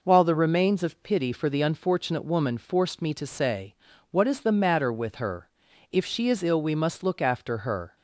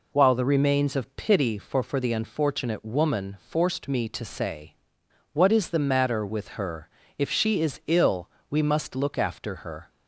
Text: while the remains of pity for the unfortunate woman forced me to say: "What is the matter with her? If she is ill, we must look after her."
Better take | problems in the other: first | says "for" twice; at 1.8 s

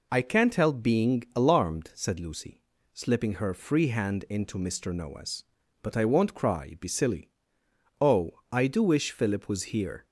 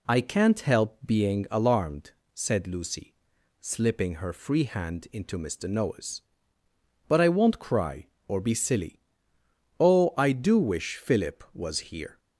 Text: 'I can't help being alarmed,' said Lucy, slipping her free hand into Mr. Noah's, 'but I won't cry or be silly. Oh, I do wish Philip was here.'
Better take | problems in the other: second | skips "or"; at 6.7 s

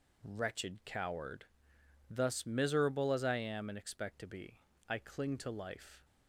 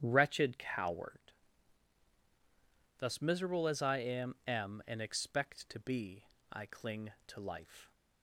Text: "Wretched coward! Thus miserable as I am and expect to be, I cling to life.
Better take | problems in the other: first | starts louder than the rest; strong; until 1.0 s; 10 dB // says "am" twice; at 4.4 s

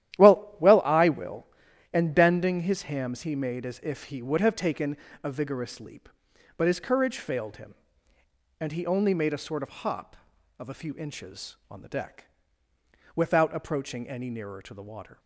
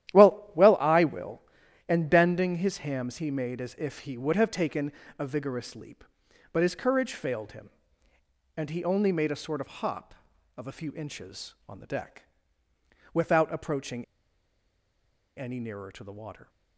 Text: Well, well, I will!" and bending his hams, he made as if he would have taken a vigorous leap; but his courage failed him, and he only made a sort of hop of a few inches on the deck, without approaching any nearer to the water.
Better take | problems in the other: first | starts louder than the rest; strong; until 1.2 s; 12 dB; strong in the first // pauses between "taken" and "a"; slight; at 4.9 s; 0.26 s long; slight in the first // pauses between "approaching" and "any"; strong; at 14.0 s; 1.3 s long

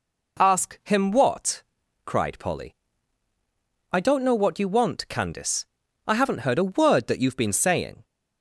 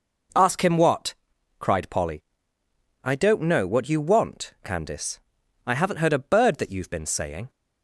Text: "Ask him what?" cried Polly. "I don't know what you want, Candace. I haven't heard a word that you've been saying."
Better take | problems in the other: first | says "bird" for "word"; at 6.2 s

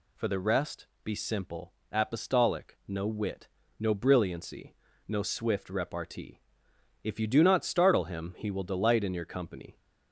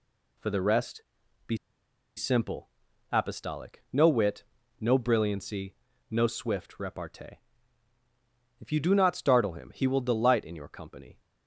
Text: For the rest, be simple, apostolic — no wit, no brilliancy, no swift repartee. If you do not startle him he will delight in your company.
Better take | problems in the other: first | pauses between "be" and "simple"; noticeable; at 1.5 s; 0.60 s long

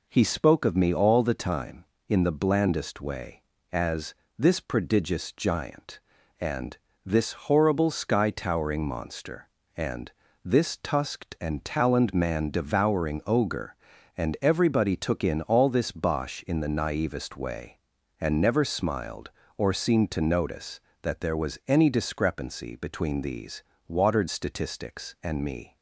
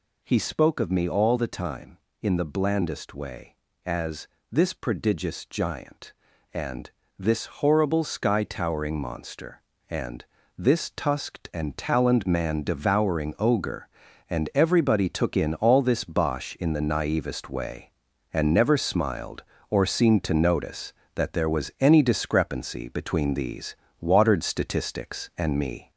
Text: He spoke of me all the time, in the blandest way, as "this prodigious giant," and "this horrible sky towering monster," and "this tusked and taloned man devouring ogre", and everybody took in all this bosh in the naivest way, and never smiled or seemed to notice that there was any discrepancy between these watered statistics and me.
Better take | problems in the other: first | gets louder; throughout; 3.5 dB // pauses between "as" and "this"; slight; at 4.2 s; 0.24 s long; slight in the first // pauses between "and" and "this"; slight; at 6.9 s; 0.28 s long; slight in the first // pauses between "and" and "this"; slight; at 10.2 s; 0.34 s long; slight in the first // pauses between "these" and "watered"; slight; at 23.7 s; 0.28 s long; slight in the first

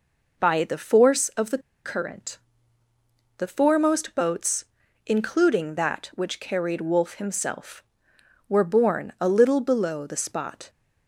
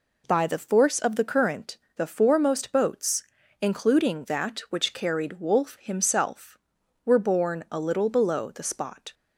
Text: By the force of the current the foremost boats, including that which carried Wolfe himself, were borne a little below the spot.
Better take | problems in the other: second | pauses between "the" and "current"; slight; at 1.5 s; 0.26 s long // pauses between "current" and "the"; at 2.3 s; 1.0 s long; slight in the second

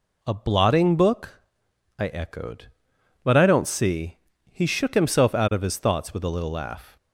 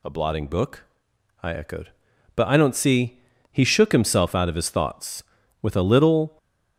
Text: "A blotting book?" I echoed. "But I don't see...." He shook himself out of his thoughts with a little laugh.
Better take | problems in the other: first | stops before "laugh"; at 6.3 s

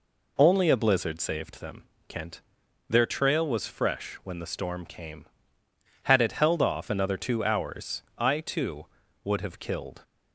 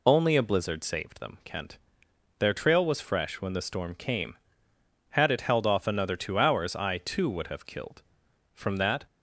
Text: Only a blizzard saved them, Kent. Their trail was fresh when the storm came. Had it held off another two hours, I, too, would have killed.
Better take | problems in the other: first | goes on to say "From that"; from 8.5 s on; 0.50 s long

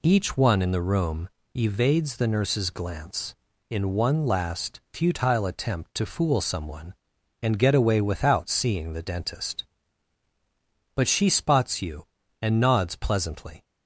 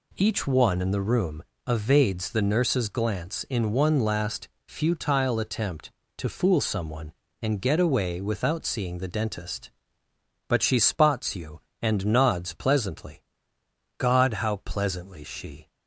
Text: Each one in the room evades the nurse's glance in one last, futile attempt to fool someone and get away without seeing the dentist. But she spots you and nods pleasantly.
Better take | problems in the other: first | pauses between "room" and "evades"; slight; at 1.4 s; 0.24 s long; slight in the first // goes on to say "God how pleasantly she"; strong; from 13.9 s on; 1.7 s long

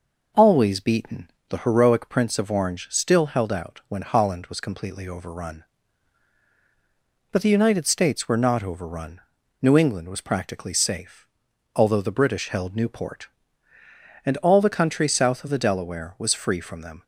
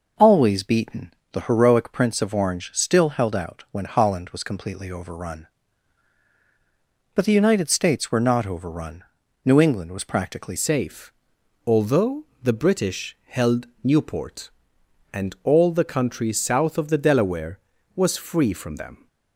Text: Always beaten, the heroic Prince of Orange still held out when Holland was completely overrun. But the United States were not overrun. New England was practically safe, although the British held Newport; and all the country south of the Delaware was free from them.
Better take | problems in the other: first | changes voice at "safe"; from 10.5 s on; 8.5 s long // pauses between "although" and "the"; slight; at 12.2 s; 0.20 s long // pauses between "held" and "Newport"; slight; at 13.6 s; 0.16 s long

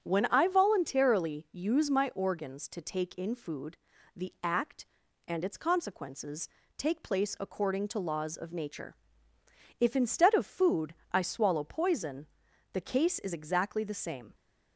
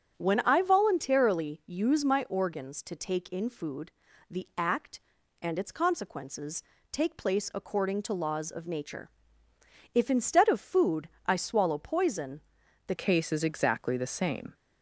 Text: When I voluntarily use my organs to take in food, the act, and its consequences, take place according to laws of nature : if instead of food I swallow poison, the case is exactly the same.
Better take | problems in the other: first | starts louder than the rest; strong; until 1.1 s; 7 dB; strong in the first // pauses between "food" and "I"; slight; at 11.0 s; 0.18 s long; slight in the first // changes voice at "case"; from 12.9 s on; 1.6 s long

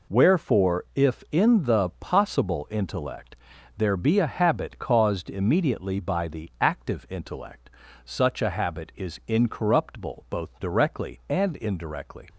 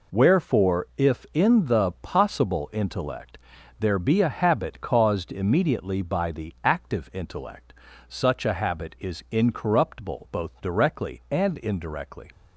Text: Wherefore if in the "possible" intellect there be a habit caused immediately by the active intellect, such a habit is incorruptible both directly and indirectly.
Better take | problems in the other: neither | pauses between "intellect" and "there"; the same in both

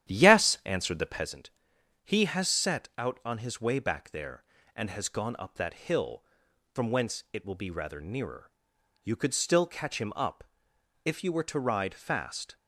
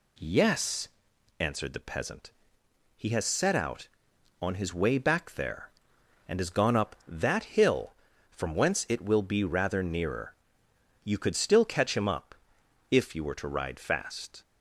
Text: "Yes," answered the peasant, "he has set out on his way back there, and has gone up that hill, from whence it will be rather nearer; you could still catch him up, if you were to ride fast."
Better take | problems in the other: second | starts louder than the rest; strong; until 1.3 s; 11 dB

